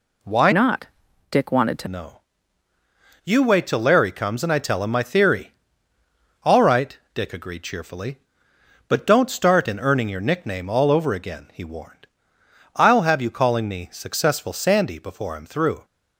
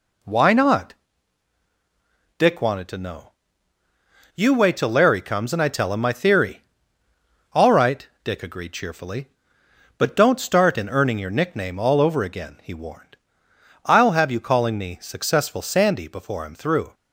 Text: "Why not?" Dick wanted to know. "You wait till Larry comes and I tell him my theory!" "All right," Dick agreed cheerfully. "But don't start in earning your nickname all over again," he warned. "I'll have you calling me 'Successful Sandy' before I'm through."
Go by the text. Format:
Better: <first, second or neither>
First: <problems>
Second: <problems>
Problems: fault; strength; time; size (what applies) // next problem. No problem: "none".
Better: second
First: changes voice from "not" to "to"; from 0.5 to 1.8 s; 1.3 s long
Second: none